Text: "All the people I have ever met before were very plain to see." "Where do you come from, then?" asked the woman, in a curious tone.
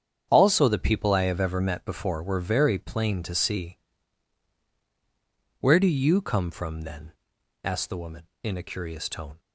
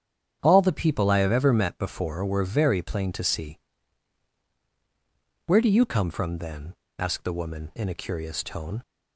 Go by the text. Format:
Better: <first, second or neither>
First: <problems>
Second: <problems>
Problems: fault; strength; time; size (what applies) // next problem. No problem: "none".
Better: second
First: starts louder than the rest; strong; until 1.3 s; 8 dB // says "Also" for "All"; at 0.2 s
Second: starts louder than the rest; strong; until 1.4 s; 8.5 dB